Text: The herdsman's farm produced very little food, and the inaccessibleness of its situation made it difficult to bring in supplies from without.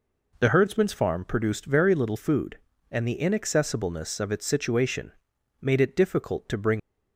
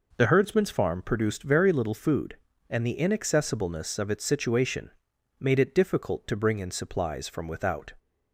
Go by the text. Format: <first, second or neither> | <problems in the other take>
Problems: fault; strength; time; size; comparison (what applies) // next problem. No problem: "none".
second | pauses between "situation" and "made"; noticeable; at 5.1 s; 0.48 s long; noticeable in the second // stops before "in supplies from without"; at 6.7 s